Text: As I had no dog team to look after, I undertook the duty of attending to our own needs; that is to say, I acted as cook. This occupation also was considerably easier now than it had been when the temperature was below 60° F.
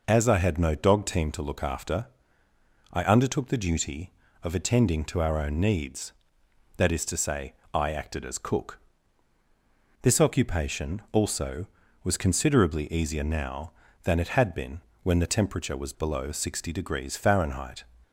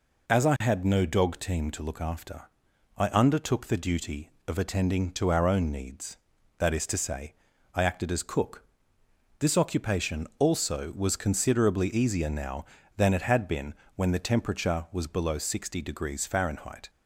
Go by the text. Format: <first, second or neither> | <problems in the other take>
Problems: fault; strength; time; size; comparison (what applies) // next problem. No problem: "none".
neither | pauses between "been" and "when"; slight; the same in both